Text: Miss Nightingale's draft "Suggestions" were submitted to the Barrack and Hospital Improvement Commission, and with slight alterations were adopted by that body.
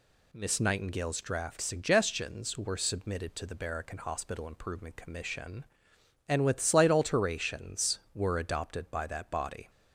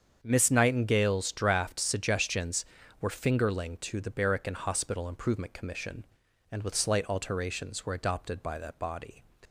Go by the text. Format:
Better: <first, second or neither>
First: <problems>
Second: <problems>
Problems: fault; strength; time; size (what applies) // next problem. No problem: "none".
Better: first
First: none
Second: starts louder than the rest; strong; until 1.2 s; 7.5 dB // says "fingerling" for "submitted"; at 3.0 s